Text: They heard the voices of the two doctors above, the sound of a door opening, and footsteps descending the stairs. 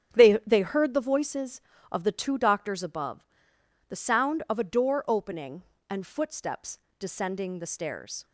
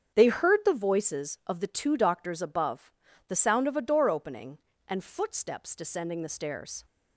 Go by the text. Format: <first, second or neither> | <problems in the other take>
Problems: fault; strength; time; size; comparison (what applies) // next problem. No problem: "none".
second | starts louder than the rest; strong; until 1.1 s; 9 dB; strong in the second // says "They" twice; at 0.4 s // pauses between "footsteps" and "descending"; slight; at 6.7 s; 0.20 s long